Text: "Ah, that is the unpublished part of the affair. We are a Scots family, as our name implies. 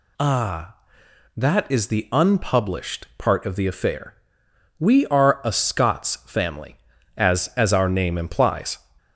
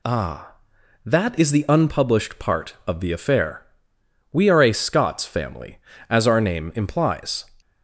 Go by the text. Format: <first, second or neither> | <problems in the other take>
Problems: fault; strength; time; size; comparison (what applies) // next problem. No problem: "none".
second | says "as" twice; at 7.5 s